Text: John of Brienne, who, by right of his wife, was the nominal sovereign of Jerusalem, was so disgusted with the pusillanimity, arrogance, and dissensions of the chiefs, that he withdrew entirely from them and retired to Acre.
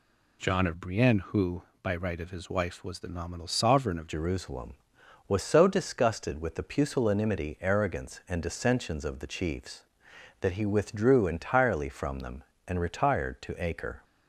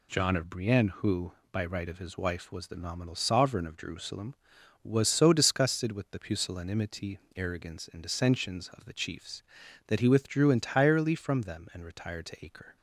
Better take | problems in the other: second | changes voice at "Jerusalem"; from 4.0 s on; 10.0 s long

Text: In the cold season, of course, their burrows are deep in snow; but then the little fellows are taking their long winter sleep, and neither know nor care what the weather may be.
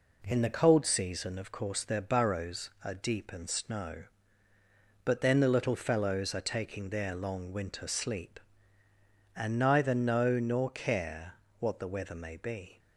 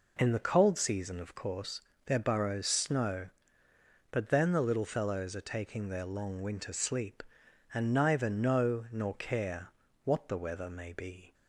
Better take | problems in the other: first | skips "are deep in"; at 2.6 s // pauses between "care" and "what"; at 9.6 s; 0.38 s long; slight in the first

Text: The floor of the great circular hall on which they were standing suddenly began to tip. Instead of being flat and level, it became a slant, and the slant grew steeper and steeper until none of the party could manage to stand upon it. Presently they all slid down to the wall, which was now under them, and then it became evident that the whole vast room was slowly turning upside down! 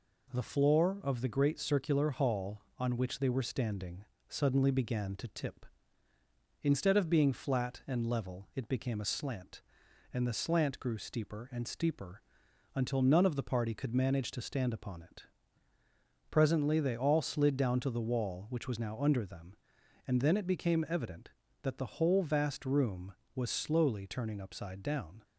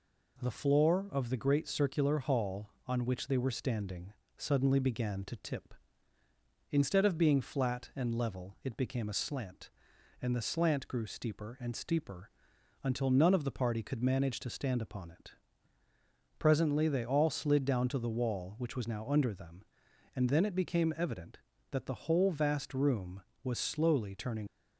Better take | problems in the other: first | pauses between "standing" and "suddenly"; slight; at 4.1 s; 0.24 s long; slight in the first // pauses between "steeper" and "until"; noticeable; at 12.2 s; 0.54 s long; noticeable in the first // stops before "upside down"; at 24.4 s

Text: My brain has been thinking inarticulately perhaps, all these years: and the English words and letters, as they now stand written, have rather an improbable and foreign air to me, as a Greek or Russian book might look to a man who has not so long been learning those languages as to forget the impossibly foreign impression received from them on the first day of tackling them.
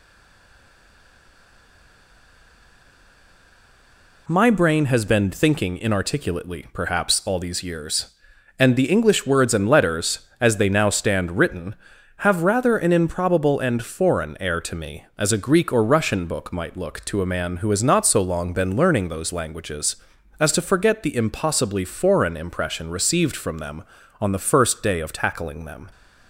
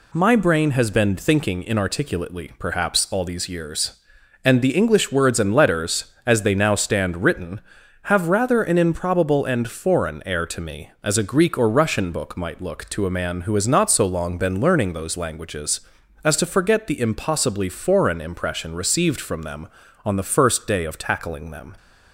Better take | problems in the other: second | stays silent before the first word; strong; until 4.2 s; 4.2 s long

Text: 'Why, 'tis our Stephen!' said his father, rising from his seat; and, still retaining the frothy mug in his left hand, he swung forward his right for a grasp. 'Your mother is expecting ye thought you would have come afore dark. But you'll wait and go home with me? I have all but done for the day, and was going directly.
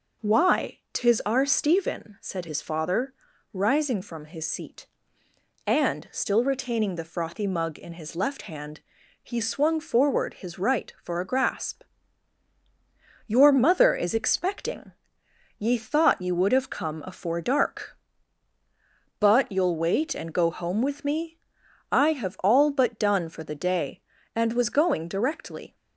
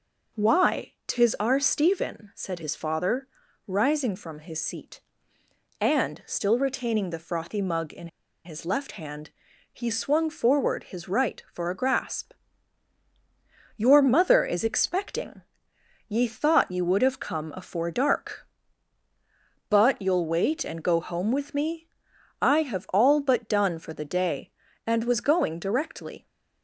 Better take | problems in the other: first | pauses between "in" and "his"; at 8.0 s; 0.37 s long // pauses between "expecting" and "ye"; noticeable; at 15.4 s; 0.68 s long; noticeable in the first

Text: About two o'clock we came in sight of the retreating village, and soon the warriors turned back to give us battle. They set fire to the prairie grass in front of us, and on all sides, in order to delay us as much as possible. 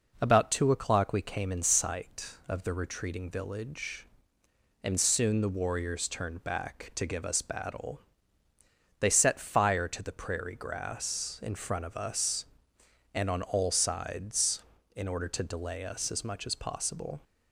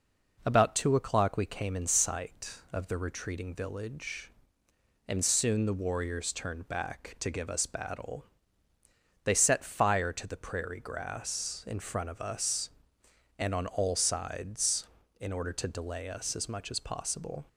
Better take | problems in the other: neither | none

